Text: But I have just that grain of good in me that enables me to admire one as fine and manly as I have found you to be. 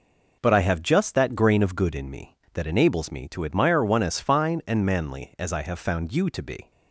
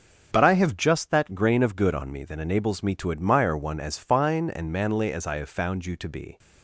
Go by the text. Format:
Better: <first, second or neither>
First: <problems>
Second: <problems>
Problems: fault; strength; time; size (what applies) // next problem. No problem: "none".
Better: first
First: none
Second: starts louder than the rest; until 1.3 s; 6 dB // says "on" for "in"; at 1.9 s